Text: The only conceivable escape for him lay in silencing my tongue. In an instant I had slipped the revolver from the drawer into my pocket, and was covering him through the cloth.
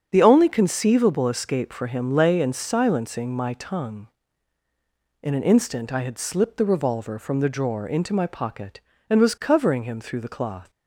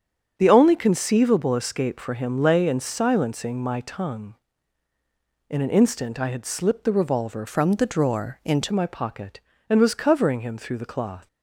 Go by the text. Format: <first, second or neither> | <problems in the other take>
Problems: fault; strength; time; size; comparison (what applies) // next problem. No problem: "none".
first | starts louder than the rest; strong; until 1.3 s; 7.5 dB; strong in the first // changes voice from "from" to "into"; from 7.4 to 8.7 s; 1.3 s long